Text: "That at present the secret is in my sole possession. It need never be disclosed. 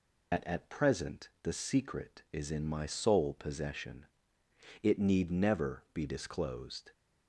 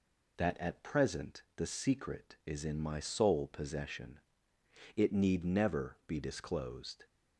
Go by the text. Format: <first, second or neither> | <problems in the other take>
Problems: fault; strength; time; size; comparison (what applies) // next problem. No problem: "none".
second | loses the start of "That"; at 0.3 s; 85 ms